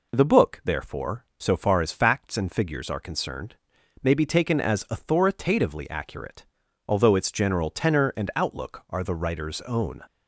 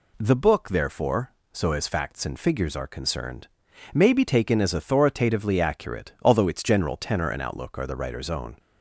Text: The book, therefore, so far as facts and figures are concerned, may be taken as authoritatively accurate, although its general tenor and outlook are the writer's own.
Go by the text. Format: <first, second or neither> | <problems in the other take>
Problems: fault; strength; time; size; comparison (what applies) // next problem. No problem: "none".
first | skips "far"; at 1.7 s